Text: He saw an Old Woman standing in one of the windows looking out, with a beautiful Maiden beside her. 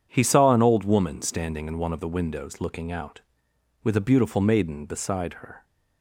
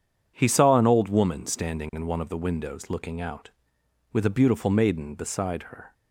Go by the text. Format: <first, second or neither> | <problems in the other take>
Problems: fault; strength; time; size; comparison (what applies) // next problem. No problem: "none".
neither | none